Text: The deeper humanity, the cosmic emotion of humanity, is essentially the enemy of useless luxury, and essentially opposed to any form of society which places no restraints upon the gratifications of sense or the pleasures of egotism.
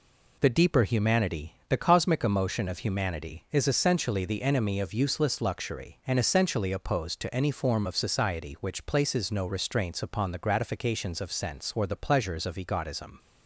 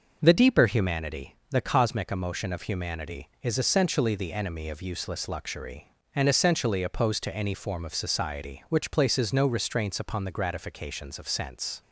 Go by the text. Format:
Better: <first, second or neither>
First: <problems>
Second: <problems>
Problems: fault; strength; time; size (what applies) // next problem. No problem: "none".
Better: first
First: none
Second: stops before "or the pleasures of egotism"; at 11.8 s